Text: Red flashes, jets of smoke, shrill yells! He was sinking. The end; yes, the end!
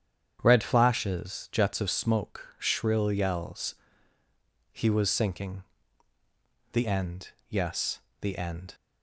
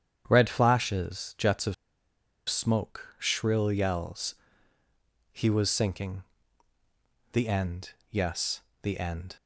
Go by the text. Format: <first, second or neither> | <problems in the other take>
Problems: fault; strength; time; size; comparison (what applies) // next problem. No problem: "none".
first | starts louder than the rest; strong; until 1.2 s; 8.5 dB; strong in the first // pauses between "of" and "smoke"; noticeable; at 1.7 s; 0.73 s long